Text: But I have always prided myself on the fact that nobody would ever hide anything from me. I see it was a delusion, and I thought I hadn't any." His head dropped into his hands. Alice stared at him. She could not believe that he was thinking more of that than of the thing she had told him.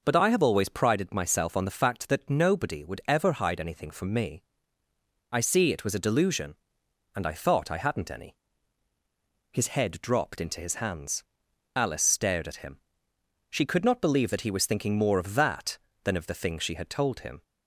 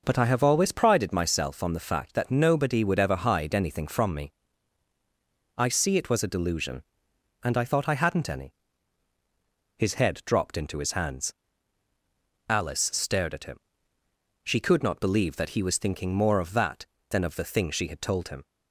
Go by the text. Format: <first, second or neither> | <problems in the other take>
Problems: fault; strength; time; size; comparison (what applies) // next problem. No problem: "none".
neither | none